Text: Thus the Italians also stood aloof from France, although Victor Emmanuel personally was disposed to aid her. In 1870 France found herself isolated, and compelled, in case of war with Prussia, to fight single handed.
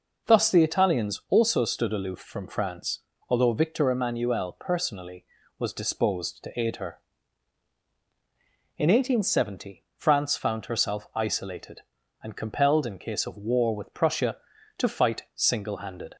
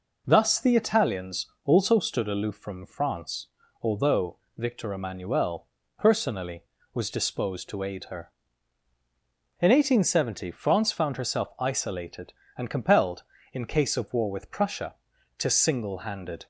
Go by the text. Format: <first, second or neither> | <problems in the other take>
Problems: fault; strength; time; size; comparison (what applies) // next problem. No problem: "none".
first | pauses between "Italians" and "also"; slight; at 1.4 s; 0.18 s long // pauses between "although" and "Victor"; slight; at 4.3 s; 0.20 s long // pauses between "Emmanuel" and "personally"; slight; at 5.6 s; 0.32 s long // skips "fight"; at 15.5 s